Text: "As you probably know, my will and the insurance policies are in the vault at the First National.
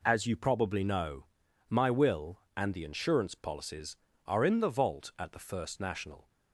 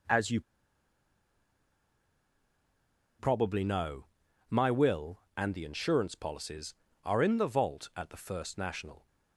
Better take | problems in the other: first | pauses between "you" and "probably"; strong; at 0.4 s; 2.7 s long

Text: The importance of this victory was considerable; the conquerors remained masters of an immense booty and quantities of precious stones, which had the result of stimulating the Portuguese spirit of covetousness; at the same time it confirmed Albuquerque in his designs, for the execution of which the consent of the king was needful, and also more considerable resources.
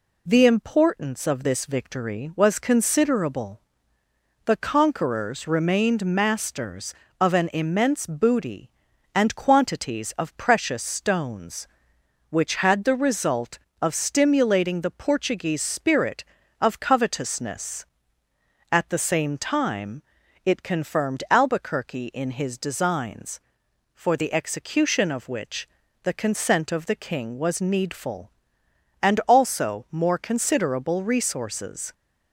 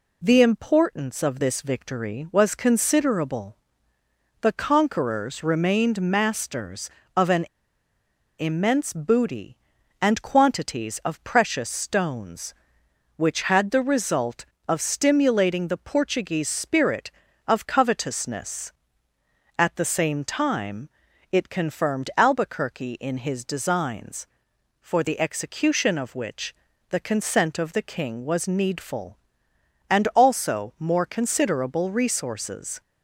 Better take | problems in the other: first | pauses between "an" and "immense"; noticeable; at 7.4 s; 0.96 s long // pauses between "time" and "it"; at 20.8 s; 0.42 s long; also in the first // pauses between "which" and "the"; slight; at 26.5 s; 0.34 s long; slight in the first

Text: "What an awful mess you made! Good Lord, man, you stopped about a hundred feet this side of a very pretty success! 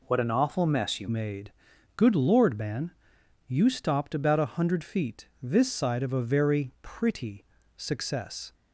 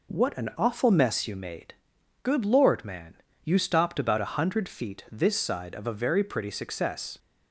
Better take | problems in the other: second | changes voice at "made"; from 1.0 s on; 7.5 s long // pauses between "pretty" and "success"; slight; at 7.4 s; 0.32 s long

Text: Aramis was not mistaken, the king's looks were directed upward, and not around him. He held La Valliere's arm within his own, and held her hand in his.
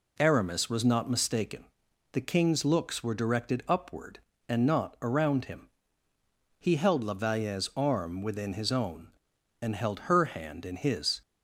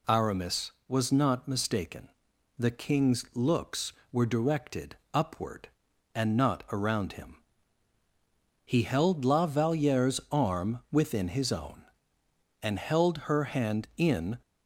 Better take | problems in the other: first | pauses between "directed" and "upward"; slight; at 4.9 s; 0.20 s long // stops before "his"; at 14.4 s

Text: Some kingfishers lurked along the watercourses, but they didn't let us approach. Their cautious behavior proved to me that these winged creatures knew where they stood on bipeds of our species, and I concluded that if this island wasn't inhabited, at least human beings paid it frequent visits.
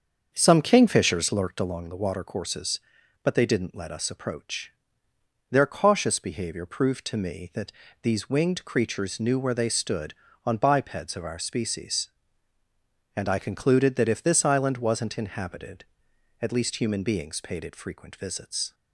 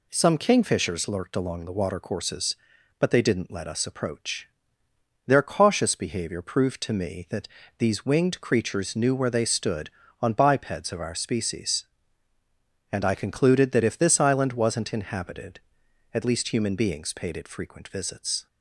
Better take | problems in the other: second | starts louder than the rest; until 1.7 s; 7 dB // pauses between "that" and "these"; slight; at 7.7 s; 0.30 s long; slight in the second

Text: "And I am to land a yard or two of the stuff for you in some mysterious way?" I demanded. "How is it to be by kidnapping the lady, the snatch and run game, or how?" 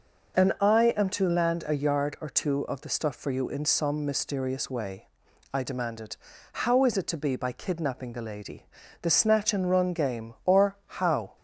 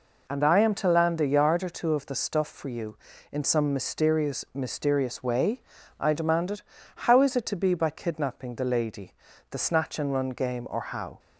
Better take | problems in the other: first | says "mysterious" twice; at 4.5 s

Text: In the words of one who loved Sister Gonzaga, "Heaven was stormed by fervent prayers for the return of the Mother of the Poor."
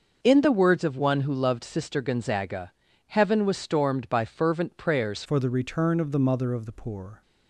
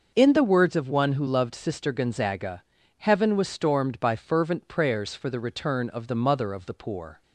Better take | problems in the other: second | starts louder than the rest; noticeable; until 1.2 s; 6 dB; noticeable in the second // changes voice at "for"; from 5.2 s on; 2.0 s long

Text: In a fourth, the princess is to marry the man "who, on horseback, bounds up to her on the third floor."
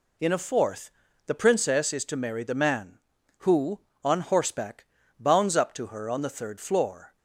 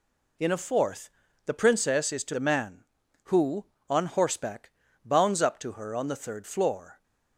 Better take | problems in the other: first | skips "marry"; at 2.3 s

